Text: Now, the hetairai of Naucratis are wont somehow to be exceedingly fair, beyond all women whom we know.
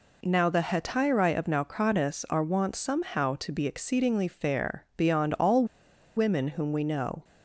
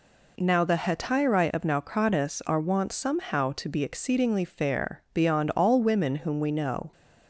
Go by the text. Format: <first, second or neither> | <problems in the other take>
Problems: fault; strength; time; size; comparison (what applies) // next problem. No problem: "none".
second | pauses between "all" and "women"; noticeable; at 5.6 s; 0.51 s long